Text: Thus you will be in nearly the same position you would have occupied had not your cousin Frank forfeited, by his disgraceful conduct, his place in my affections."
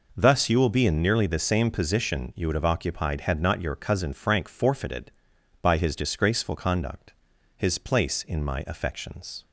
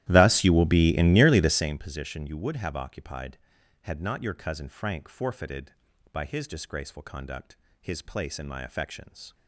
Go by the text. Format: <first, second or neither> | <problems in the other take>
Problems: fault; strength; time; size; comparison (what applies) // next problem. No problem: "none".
first | starts louder than the rest; strong; until 1.8 s; 13.5 dB